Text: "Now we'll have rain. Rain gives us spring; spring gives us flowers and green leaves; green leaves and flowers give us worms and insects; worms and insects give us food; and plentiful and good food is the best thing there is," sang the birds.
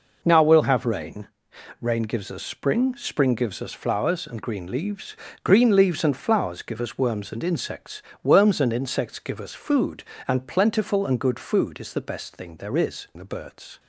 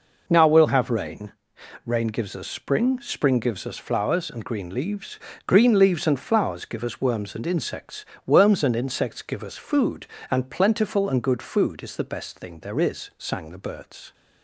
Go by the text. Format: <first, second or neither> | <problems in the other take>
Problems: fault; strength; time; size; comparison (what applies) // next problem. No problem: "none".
second | skips "sang"; at 13.1 s